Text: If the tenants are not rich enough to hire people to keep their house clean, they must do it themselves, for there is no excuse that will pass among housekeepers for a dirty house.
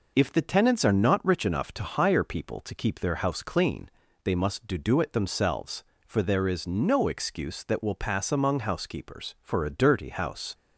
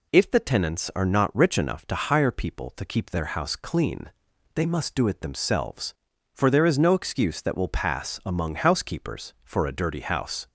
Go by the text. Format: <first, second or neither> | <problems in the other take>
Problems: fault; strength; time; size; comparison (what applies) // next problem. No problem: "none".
second | says "do" twice; at 4.7 s